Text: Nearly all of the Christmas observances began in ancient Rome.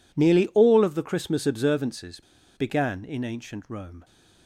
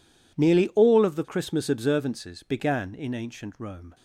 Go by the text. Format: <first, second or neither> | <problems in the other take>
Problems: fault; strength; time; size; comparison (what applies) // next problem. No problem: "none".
second | pauses between "observances" and "began"; slight; at 2.2 s; 0.35 s long